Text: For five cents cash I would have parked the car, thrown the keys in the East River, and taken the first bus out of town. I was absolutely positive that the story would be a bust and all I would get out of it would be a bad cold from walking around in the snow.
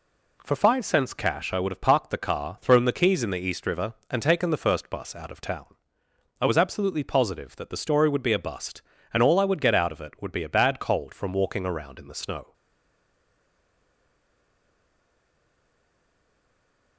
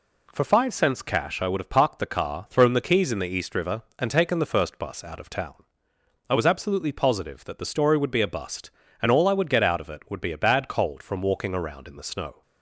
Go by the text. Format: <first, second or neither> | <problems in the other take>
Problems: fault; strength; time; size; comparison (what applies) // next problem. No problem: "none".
second | stays silent after the last word; strong; from 12.5 s on; 4.4 s long